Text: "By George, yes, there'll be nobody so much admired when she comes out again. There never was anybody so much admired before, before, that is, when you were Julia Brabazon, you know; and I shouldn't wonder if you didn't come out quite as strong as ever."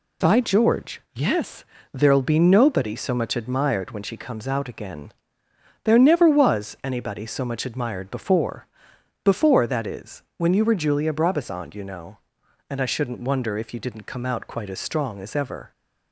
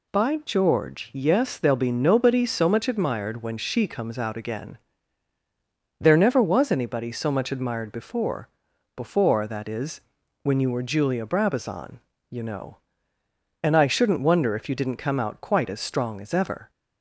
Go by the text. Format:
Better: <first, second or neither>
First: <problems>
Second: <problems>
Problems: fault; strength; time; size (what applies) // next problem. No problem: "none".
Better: neither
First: none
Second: none